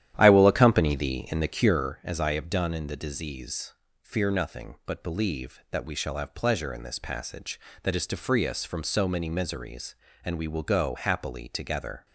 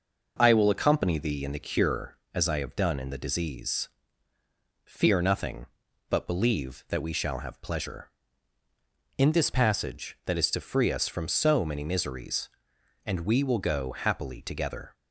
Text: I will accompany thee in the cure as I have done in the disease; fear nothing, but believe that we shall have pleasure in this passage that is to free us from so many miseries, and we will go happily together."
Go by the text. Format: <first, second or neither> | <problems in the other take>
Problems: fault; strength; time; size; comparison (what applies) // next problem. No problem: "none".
second | starts louder than the rest; strong; until 1.8 s; 11.5 dB